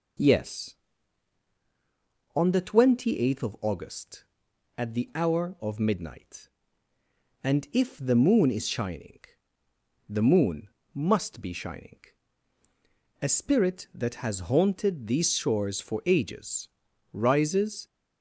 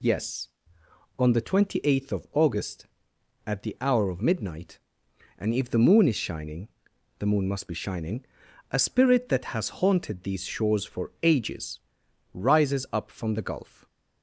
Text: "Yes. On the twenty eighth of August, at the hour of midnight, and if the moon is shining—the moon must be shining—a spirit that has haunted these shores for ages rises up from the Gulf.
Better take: second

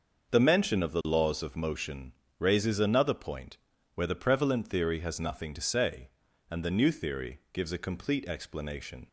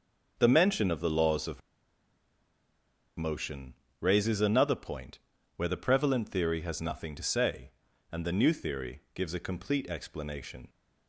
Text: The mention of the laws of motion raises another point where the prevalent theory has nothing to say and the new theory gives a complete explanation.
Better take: first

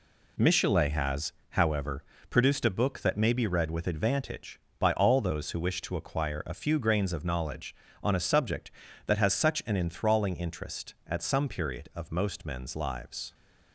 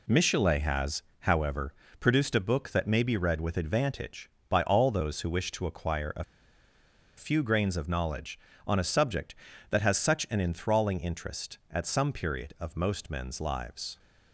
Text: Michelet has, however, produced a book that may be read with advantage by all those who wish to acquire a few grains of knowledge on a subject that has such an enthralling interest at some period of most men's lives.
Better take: first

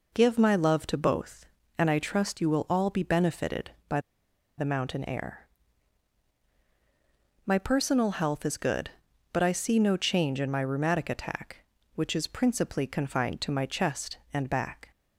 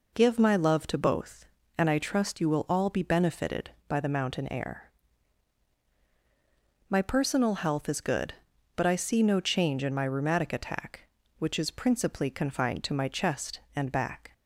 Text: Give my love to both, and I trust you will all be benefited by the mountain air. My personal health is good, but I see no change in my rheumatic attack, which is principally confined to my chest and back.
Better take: second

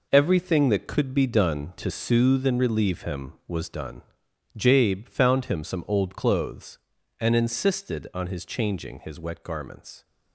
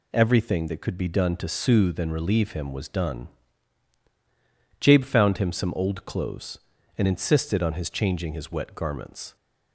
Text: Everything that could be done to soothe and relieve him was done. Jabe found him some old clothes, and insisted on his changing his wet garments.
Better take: second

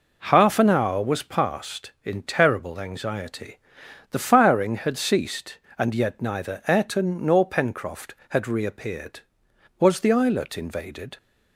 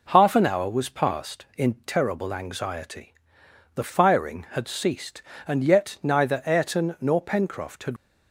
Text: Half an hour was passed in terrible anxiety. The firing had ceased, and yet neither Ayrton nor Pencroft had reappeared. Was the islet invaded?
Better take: first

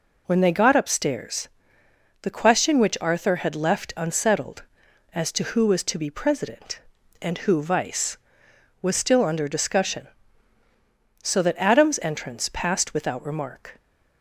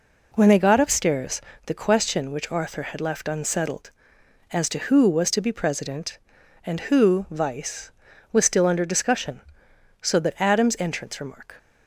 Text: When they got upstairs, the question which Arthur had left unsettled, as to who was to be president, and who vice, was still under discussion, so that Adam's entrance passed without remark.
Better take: first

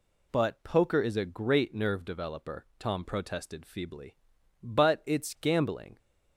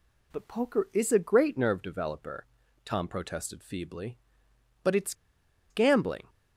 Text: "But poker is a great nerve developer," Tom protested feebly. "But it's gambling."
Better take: first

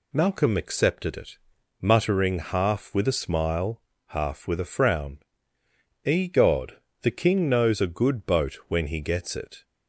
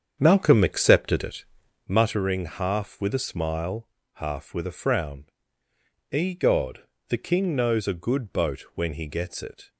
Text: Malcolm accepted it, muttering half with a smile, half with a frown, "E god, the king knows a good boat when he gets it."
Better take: first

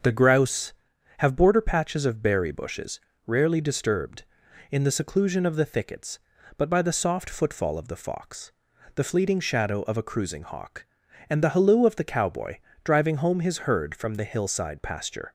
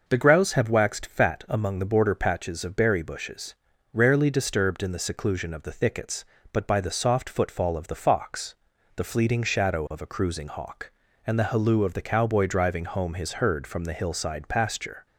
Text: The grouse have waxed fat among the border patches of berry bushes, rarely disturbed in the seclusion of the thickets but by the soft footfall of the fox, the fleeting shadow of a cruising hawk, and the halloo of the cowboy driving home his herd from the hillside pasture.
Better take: second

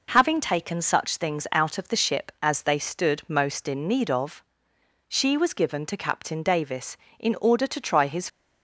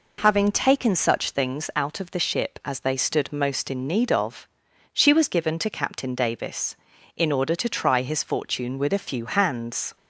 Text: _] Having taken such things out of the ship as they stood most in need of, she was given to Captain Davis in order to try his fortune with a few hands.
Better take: second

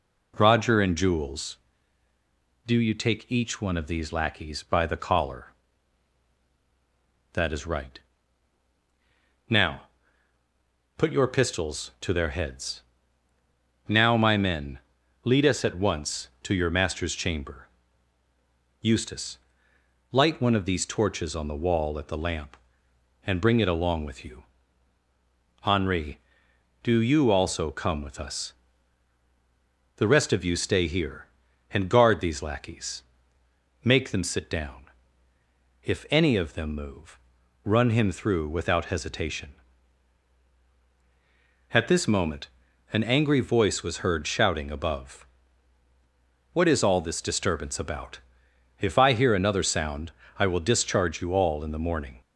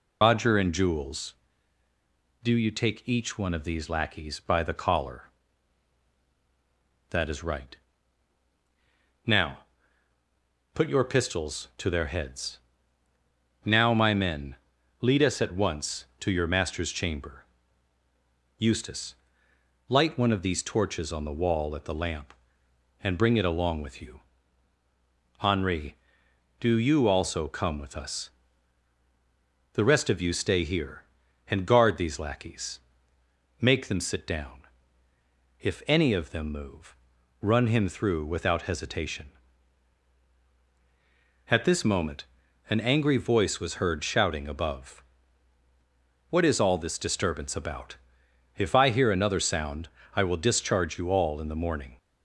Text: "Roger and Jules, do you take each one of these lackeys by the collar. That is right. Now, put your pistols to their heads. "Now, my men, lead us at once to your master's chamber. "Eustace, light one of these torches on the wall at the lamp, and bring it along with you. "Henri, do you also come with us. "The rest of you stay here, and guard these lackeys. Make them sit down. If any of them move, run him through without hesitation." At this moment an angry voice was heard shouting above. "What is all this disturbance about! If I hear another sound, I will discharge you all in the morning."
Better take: first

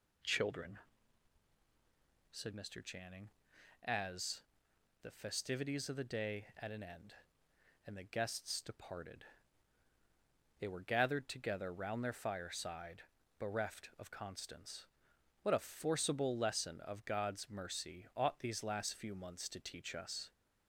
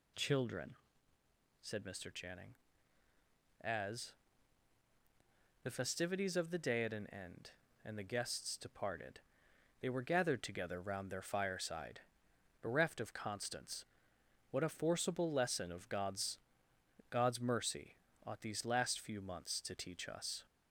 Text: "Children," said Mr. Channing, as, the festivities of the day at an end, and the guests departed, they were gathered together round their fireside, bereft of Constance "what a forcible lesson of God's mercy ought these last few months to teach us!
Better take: first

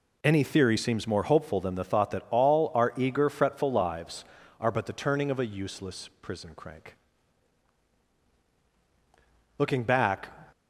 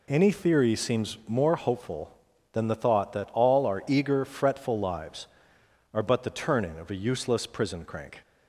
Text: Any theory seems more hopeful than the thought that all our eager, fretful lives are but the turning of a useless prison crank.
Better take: second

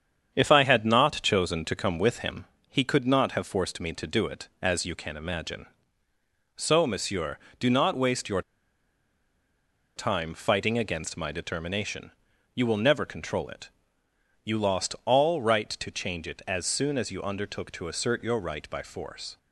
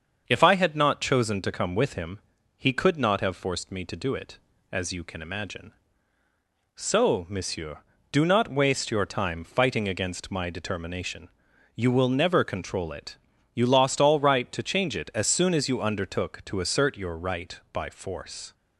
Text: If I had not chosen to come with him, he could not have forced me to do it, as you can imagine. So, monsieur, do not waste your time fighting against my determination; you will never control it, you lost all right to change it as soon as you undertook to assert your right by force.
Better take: second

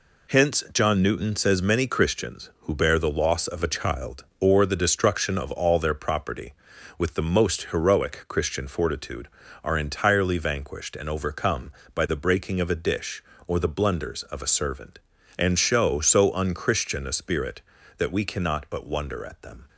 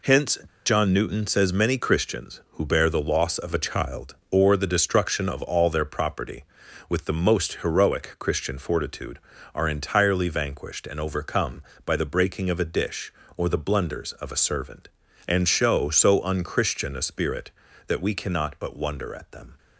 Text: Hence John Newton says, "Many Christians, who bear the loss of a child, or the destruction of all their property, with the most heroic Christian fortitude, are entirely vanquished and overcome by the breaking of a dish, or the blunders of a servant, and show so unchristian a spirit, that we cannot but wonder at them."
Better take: first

